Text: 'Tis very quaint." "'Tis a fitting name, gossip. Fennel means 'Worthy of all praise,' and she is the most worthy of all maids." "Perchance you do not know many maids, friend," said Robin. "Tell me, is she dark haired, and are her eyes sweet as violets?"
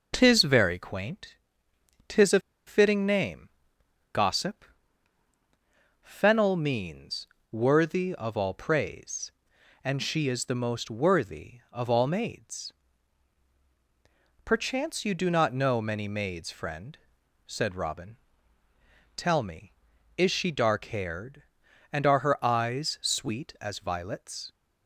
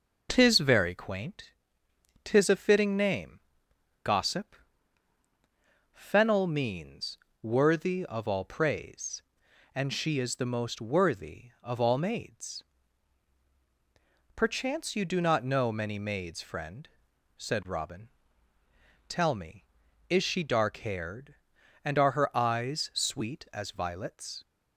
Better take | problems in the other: second | pauses between "a" and "fitting"; slight; at 2.3 s; 0.28 s long // pauses between "means" and "Worthy"; slight; at 7.2 s; 0.24 s long; slight in the second

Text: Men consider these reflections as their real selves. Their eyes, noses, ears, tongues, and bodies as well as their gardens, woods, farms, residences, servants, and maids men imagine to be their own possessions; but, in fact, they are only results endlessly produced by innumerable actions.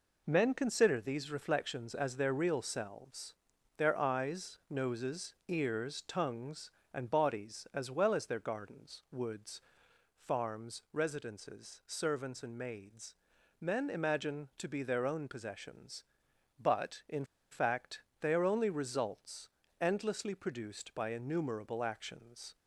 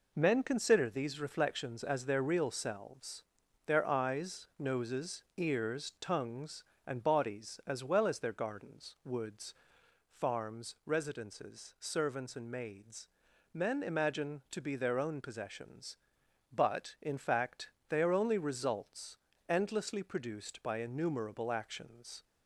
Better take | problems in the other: second | pauses between "maids" and "men"; at 13.1 s; 0.44 s long; also in the second // pauses between "in" and "fact"; slight; at 17.2 s; 0.27 s long // pauses between "results" and "endlessly"; slight; at 19.4 s; 0.30 s long; slight in the second

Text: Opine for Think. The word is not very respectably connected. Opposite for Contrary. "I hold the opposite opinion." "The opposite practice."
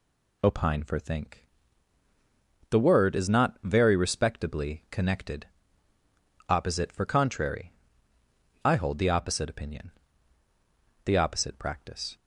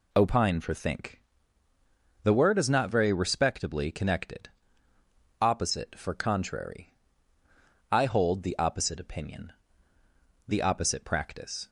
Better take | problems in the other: neither | none

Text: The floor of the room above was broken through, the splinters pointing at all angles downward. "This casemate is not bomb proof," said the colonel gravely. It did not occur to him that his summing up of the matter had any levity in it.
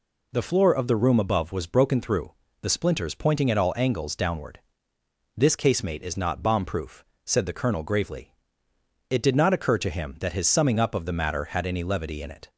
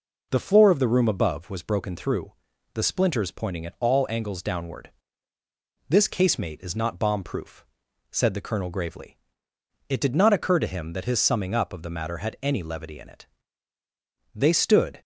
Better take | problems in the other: first | goes on to say "They stood"; noticeable; from 14.3 s on; 0.66 s long

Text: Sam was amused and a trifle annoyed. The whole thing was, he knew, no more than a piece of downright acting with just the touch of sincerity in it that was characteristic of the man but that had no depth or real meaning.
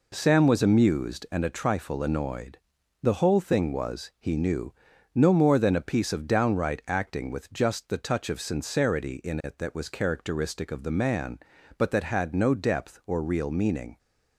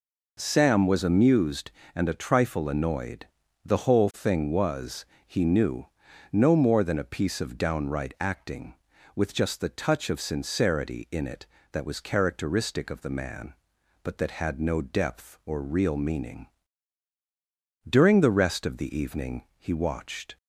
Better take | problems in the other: first | goes on to say "During the rest of the evening he watched"; strong; from 17.8 s on; 2.5 s long

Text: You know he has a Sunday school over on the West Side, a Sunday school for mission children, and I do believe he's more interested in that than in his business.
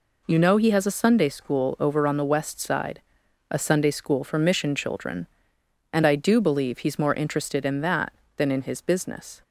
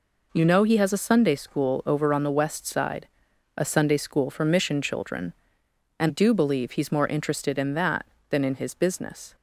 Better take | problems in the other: first | skips "I"; at 6.0 s

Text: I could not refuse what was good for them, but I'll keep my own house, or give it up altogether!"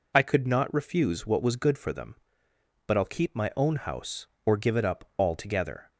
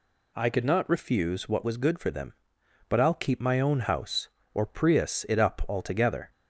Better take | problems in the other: first | says "prius" for "give"; at 4.6 s

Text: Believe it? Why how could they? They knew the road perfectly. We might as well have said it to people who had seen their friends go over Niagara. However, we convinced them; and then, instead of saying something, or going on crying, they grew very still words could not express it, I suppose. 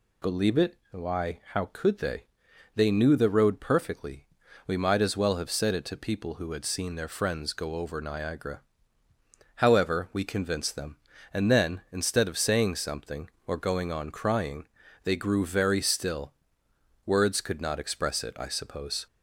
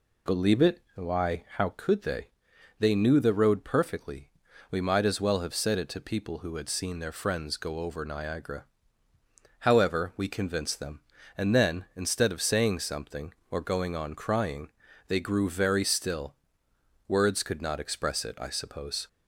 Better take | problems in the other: first | starts louder than the rest; slight; until 1.9 s; 2 dB // pauses between "still" and "words"; noticeable; at 16.3 s; 0.74 s long; noticeable in the first

